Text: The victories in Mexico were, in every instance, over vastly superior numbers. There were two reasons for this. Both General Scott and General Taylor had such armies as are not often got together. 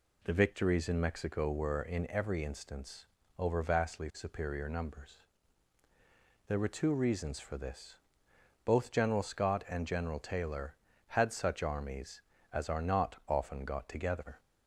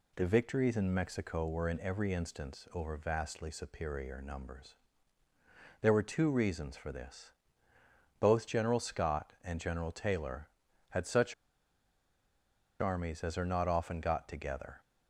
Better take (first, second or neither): first